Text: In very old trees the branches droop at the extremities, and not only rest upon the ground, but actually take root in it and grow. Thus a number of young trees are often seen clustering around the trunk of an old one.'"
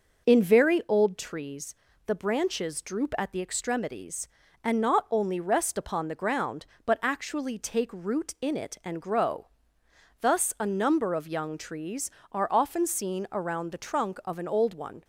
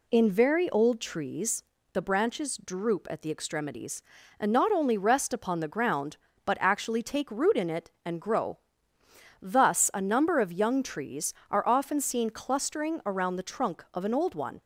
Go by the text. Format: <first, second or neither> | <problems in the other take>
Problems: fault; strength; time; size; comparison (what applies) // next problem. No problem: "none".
second | pauses between "trees" and "the"; slight; at 1.7 s; 0.32 s long; slight in the second // skips "clustering"; at 13.2 s